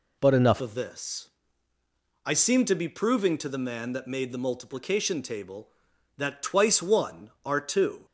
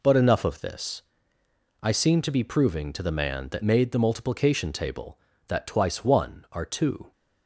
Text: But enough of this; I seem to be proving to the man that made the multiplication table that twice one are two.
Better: second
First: changes voice at "of"; from 0.5 s on; 7.5 s long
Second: none

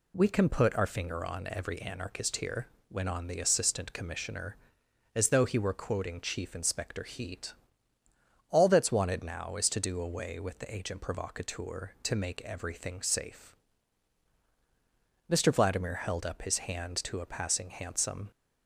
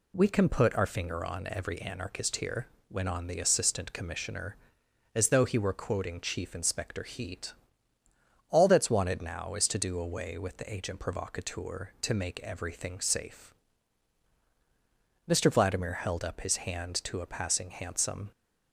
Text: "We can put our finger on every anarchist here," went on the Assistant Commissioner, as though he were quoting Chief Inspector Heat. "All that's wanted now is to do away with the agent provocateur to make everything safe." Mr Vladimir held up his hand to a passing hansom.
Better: neither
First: none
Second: none

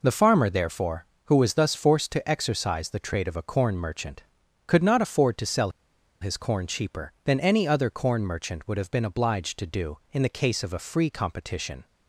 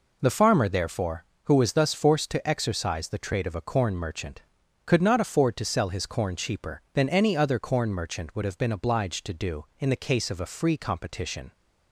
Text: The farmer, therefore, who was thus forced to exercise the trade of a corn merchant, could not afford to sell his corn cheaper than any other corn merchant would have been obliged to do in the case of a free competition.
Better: second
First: pauses between "sell" and "his"; noticeable; at 5.6 s; 0.52 s long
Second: none

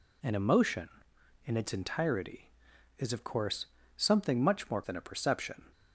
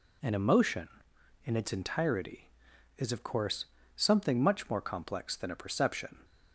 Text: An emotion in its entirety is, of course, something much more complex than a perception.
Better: second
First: skips "complex"; at 4.8 s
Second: none

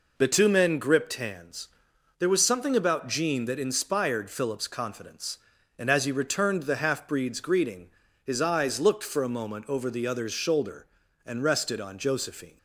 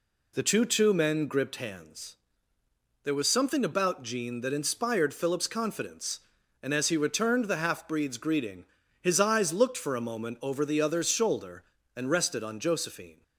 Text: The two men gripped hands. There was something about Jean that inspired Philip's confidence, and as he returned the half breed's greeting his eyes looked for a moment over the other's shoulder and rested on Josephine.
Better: first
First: pauses between "greeting" and "his"; slight; at 7.8 s; 0.34 s long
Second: says "two" twice; at 0.6 s // pauses between "greeting" and "his"; at 8.6 s; 0.38 s long

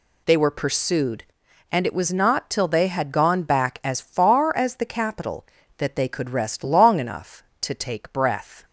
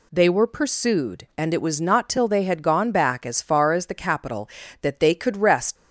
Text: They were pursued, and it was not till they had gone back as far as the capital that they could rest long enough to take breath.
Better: first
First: none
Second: stops before "long enough to take breath"; at 5.7 s

